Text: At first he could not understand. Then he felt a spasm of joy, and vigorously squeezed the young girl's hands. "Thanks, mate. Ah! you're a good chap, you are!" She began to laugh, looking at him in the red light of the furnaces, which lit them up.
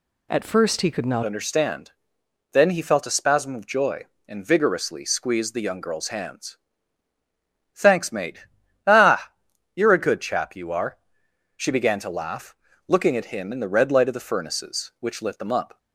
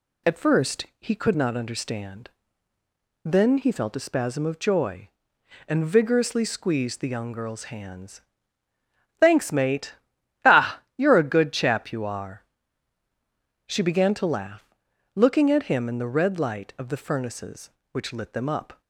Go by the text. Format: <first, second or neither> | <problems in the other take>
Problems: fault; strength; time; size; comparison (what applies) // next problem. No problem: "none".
second | changes voice at "understand"; from 1.2 s on; 14.5 s long